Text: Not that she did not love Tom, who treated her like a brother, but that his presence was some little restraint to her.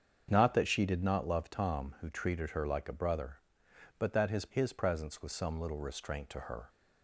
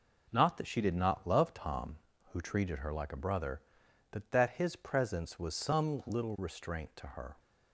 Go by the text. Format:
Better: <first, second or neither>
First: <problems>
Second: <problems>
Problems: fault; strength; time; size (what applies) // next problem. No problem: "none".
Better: second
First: starts louder than the rest; until 1.3 s; 7 dB // says "his" twice; at 4.5 s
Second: none